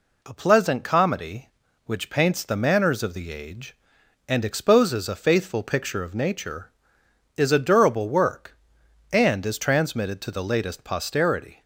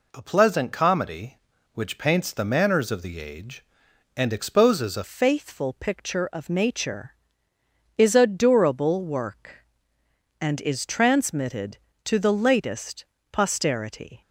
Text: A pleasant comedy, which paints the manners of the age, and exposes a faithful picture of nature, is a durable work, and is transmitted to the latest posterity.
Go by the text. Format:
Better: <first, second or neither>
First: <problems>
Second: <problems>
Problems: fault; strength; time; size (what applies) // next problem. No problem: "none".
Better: first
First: none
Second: changes voice at "faithful"; from 5.0 s on; 9.2 s long // pauses between "latest" and "posterity"; slight; at 13.0 s; 0.28 s long